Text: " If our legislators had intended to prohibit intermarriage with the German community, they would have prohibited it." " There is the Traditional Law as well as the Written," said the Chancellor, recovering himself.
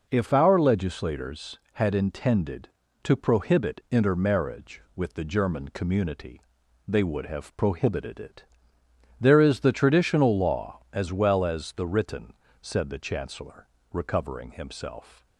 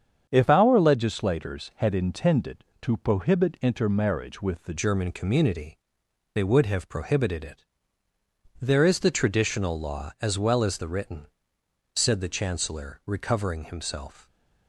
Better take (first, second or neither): first